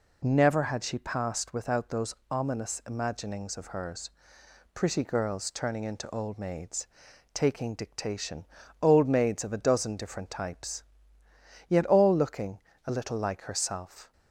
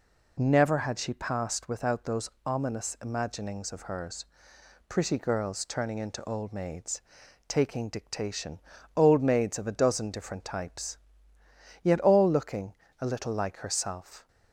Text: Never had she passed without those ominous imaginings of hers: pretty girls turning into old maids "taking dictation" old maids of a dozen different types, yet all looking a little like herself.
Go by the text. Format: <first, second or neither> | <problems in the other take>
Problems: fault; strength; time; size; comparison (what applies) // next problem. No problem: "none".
neither | pauses between "those" and "ominous"; slight; the same in both // pauses between "maids" and "taking"; noticeable; the same in both // pauses between "dictation" and "old"; slight; the same in both // pauses between "looking" and "a"; slight; the same in both